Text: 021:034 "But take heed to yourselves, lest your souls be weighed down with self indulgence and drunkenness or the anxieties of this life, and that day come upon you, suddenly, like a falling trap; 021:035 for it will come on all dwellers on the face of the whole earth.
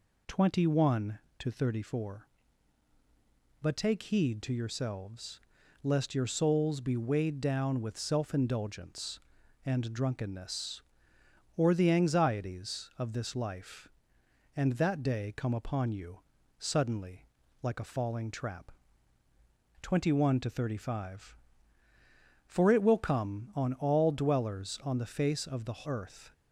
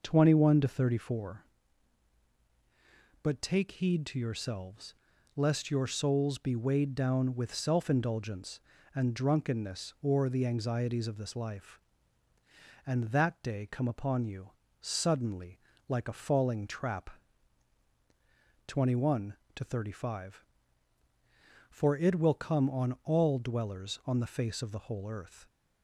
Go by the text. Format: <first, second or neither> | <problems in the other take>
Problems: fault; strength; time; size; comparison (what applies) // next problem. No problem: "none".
second | skips "whole"; at 25.8 s